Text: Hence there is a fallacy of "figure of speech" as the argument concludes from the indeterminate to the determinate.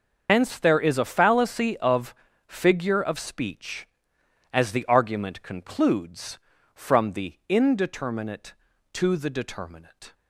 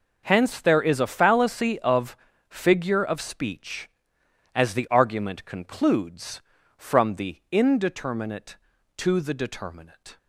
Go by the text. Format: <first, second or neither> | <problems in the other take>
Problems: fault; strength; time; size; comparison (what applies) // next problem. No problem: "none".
second | loses the start of "Hence"; at 0.2 s; 75 ms // starts louder than the rest; until 1.3 s; 6.5 dB // pauses between "of" and "figure"; slight; at 2.1 s; 0.32 s long; slight in the second